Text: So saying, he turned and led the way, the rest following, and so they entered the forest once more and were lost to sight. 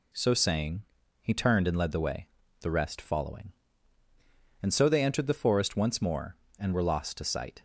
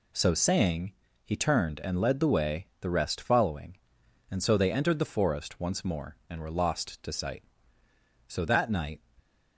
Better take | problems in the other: first | goes on to say "So that night"; noticeable; from 8.2 s on; 0.74 s long

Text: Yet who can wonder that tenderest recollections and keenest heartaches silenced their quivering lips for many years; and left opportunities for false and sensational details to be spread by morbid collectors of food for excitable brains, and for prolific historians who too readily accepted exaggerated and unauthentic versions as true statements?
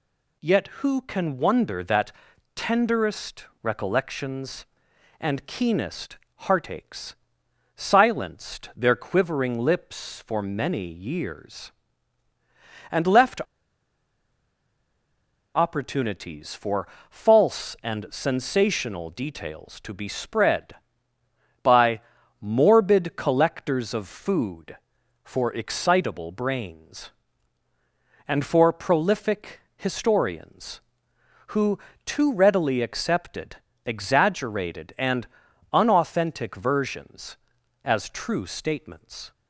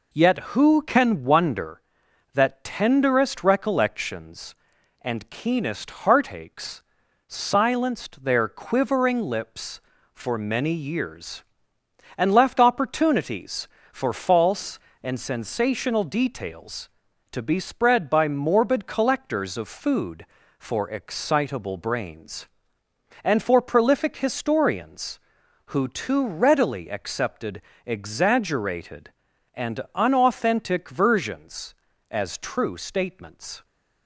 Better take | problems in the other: second | pauses between "that" and "tenderest"; at 2.1 s; 0.42 s long // pauses between "tenderest" and "recollections"; slight; at 3.4 s; 0.16 s long // pauses between "keenest" and "heartaches"; slight; at 6.1 s; 0.20 s long // pauses between "heartaches" and "silenced"; noticeable; at 7.1 s; 0.60 s long; noticeable in the second // pauses between "left" and "opportunities"; strong; at 13.4 s; 2.1 s long // pauses between "for" and "false"; slight; at 16.8 s; 0.22 s long // pauses between "by" and "morbid"; at 21.9 s; 0.40 s long // pauses between "prolific" and "historians"; slight; at 29.5 s; 0.16 s long // pauses between "who" and "too"; slight; at 31.7 s; 0.26 s long // pauses between "accepted" and "exaggerated"; slight; at 33.5 s; 0.30 s long; slight in the second // pauses between "and" and "unauthentic"; at 35.2 s; 0.44 s long

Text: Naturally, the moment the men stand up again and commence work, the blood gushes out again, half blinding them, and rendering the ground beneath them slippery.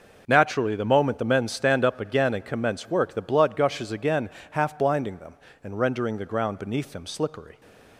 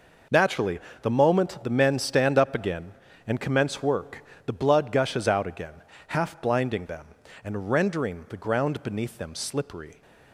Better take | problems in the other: second | skips "out"; at 3.9 s

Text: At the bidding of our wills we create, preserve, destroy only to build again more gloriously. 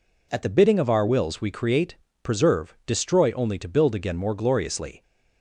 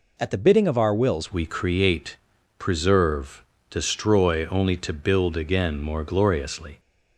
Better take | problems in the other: first | changes voice at "we"; from 1.3 s on; 5.4 s long

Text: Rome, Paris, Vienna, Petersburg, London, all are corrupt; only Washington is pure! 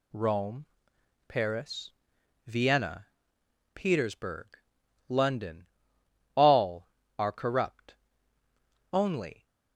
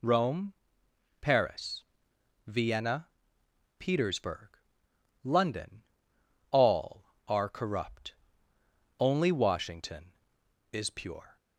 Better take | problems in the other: second | stops before "Washington is pure"; at 9.4 s

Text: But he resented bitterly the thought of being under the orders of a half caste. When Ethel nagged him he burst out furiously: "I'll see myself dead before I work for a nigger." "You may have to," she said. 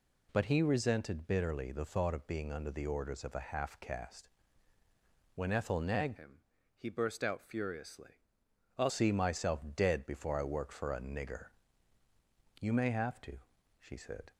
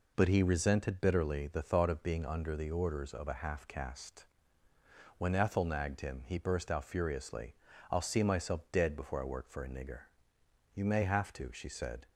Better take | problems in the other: second | changes voice from "him" to "I'll"; from 6.1 to 8.9 s; 2.8 s long // pauses between "him" and "he"; slight; at 6.3 s; 0.36 s long // pauses between "myself" and "dead"; slight; at 9.5 s; 0.16 s long

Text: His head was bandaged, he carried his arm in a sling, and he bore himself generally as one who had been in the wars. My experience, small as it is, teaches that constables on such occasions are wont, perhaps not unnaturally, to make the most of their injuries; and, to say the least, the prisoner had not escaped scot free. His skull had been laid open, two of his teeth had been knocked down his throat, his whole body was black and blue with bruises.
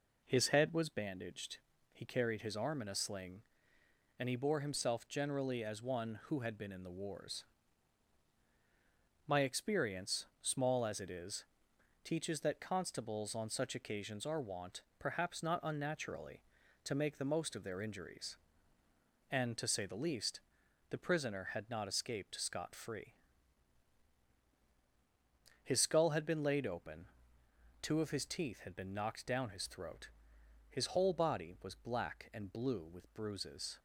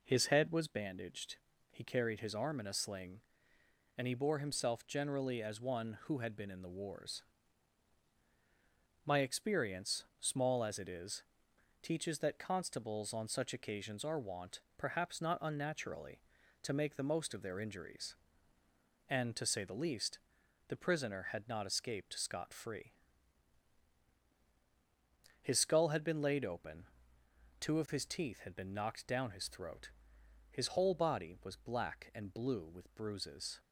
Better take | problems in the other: neither | none

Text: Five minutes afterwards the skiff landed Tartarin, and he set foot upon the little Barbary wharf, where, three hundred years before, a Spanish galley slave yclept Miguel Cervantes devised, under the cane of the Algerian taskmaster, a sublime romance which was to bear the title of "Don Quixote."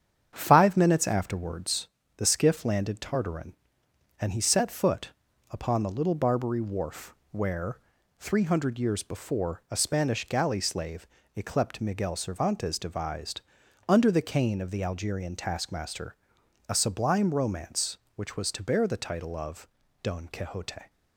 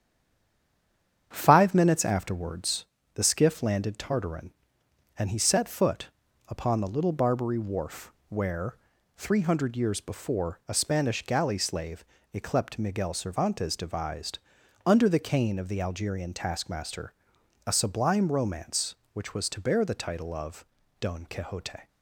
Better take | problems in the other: first | stays silent before the first word; noticeable; until 1.3 s; 1.3 s long // starts louder than the rest; strong; until 2.3 s; 8.5 dB; strong in the first // pauses between "afterwards" and "the"; slight; at 2.8 s; 0.30 s long; slight in the first // pauses between "foot" and "upon"; at 6.0 s; 0.38 s long; also in the first // pauses between "slave" and "yclept"; slight; at 12.0 s; 0.30 s long; slight in the first // pauses between "of" and "Don"; slight; at 20.6 s; 0.34 s long; slight in the first

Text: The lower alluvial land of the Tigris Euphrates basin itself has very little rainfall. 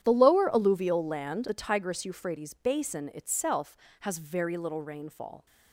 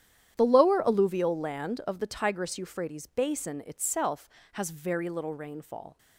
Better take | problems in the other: second | starts louder than the rest; strong; until 1.0 s; 10 dB; strong in the second // skips "of"; at 1.4 s

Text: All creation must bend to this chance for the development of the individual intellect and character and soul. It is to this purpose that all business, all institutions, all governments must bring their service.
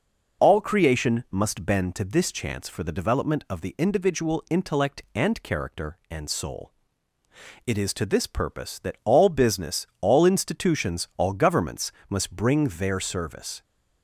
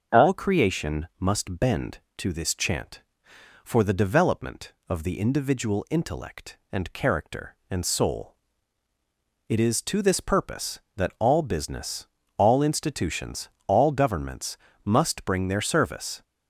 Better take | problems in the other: first | starts louder than the rest; until 1.2 s; 6.5 dB // says "chant" for "chance"; at 2.5 s // pauses between "governments" and "must"; slight; at 14.5 s; 0.26 s long; slight in the first

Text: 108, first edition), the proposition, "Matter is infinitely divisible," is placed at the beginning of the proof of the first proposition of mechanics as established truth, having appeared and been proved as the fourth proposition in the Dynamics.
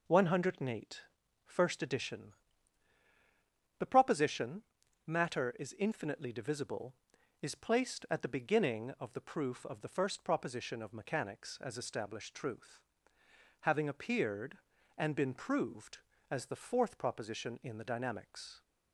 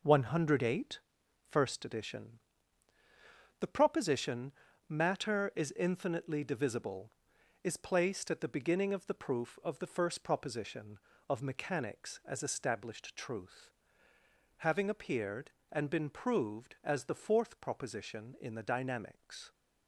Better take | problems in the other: neither | none

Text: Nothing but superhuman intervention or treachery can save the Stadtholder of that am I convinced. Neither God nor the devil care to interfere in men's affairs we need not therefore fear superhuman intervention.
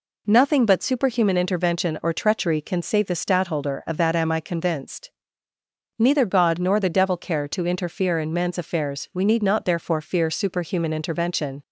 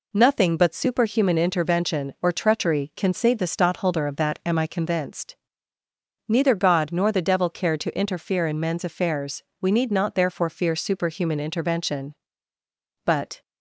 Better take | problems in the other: first | pauses between "affairs" and "we"; slight; at 9.4 s; 0.16 s long // goes on to say "But"; slight; from 13.0 s on; 0.36 s long

